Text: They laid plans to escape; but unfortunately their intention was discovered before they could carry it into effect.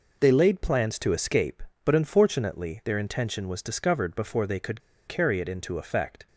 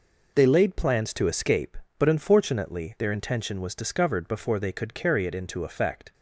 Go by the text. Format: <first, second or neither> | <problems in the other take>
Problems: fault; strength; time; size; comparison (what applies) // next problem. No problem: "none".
second | pauses between "could" and "carry"; slight; at 4.8 s; 0.26 s long